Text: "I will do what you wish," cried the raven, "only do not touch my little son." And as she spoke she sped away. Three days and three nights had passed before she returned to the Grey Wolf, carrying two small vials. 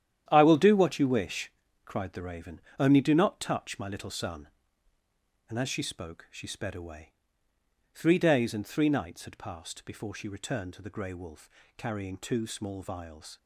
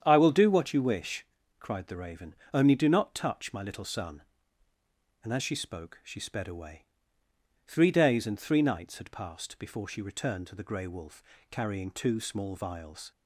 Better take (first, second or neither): second